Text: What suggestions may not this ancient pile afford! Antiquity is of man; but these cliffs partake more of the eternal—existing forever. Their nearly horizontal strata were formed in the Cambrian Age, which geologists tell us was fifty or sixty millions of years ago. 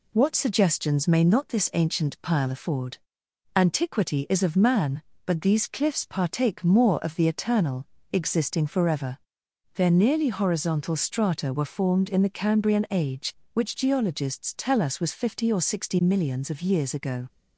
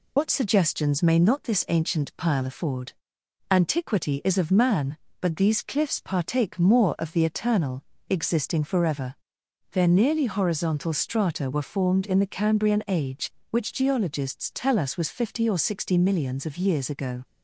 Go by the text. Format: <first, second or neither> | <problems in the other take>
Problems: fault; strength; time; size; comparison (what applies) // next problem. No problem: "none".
first | loses the start of "What"; at 0.1 s; 80 ms